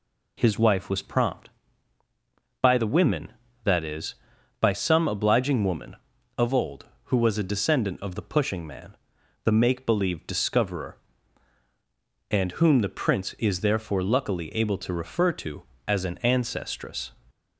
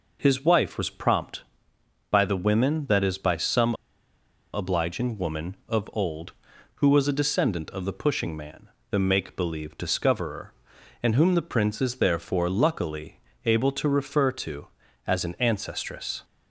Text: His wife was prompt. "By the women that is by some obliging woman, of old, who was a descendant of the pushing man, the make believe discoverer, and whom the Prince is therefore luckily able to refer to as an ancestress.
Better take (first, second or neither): first